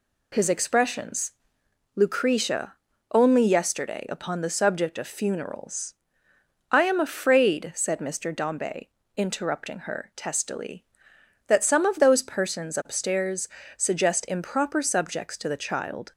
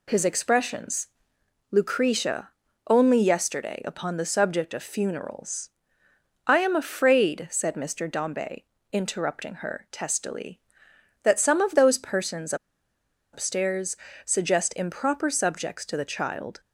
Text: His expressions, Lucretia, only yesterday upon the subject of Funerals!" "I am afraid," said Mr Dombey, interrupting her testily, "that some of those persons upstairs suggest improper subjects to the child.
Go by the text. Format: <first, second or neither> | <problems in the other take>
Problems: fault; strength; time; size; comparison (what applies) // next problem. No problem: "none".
first | pauses between "persons" and "upstairs"; noticeable; at 12.5 s; 0.78 s long // pauses between "upstairs" and "suggest"; slight; at 13.9 s; 0.30 s long; slight in the first